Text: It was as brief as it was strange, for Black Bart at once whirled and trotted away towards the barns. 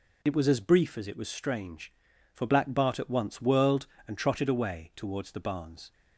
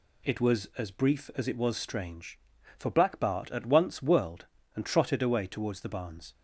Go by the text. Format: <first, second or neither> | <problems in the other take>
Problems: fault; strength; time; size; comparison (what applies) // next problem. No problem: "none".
neither | none